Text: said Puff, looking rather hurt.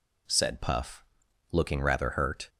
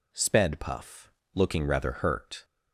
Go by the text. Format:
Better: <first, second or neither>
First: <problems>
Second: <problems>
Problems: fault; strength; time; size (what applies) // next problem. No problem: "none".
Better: first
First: none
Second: says "sped" for "said"; at 0.1 s